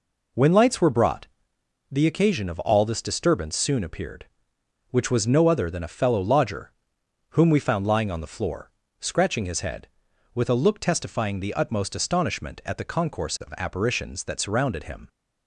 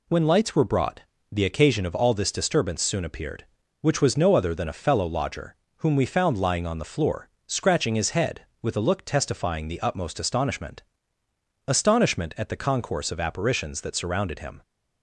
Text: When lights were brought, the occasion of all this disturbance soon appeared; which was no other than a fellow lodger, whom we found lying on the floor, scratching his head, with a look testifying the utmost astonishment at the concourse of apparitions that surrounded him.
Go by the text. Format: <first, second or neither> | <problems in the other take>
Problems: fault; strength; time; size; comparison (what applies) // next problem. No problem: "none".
first | says "astonishment" twice; at 11.6 s